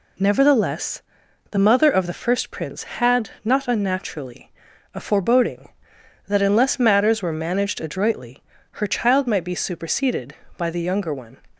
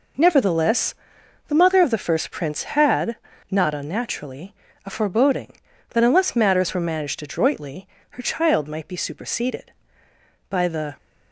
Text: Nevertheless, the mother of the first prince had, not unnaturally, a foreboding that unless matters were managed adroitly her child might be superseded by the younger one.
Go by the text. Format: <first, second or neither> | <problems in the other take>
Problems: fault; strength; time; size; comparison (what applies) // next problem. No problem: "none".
first | pauses between "adroitly" and "her"; slight; at 7.8 s; 0.24 s long; slight in the first // stops before "younger one"; at 10.9 s